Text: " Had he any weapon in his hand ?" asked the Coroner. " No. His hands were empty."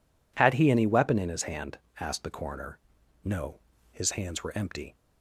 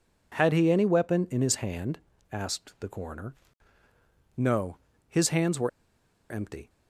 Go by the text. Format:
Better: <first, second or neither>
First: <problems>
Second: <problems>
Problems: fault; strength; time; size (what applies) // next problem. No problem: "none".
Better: first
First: none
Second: pauses between "were" and "empty"; noticeable; at 5.6 s; 0.61 s long